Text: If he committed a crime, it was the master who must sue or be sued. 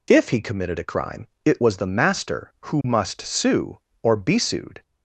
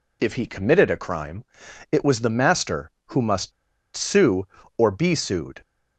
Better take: first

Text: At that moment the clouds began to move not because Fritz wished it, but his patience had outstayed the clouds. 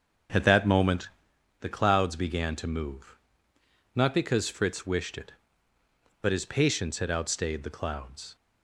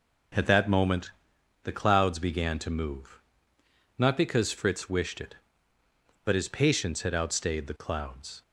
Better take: second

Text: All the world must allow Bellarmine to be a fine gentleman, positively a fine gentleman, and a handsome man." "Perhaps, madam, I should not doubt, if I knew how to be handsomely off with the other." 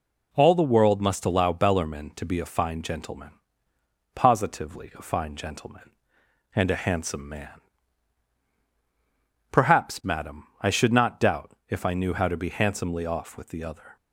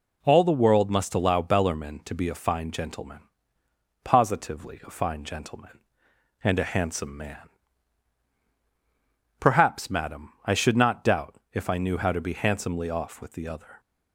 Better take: neither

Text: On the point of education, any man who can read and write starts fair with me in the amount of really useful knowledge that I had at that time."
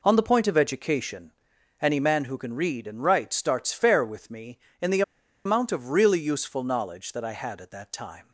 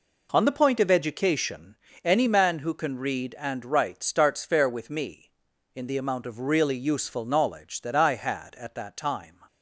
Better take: second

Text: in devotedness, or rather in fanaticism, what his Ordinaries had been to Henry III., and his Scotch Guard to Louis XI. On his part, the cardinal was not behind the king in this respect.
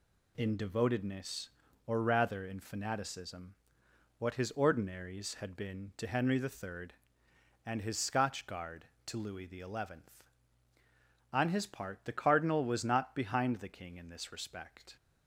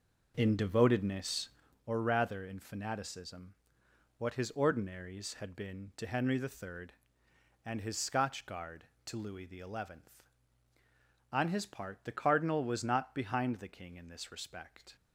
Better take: first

